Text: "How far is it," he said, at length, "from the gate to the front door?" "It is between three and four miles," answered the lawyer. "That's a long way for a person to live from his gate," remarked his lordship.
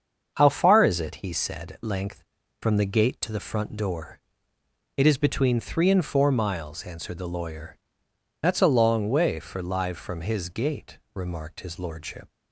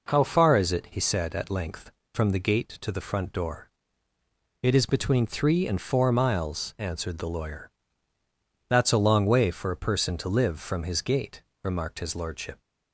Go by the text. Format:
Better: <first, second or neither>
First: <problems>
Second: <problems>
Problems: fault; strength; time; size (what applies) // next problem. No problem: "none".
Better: second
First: starts louder than the rest; until 1.3 s; 7 dB // skips "a person to"; at 9.6 s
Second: none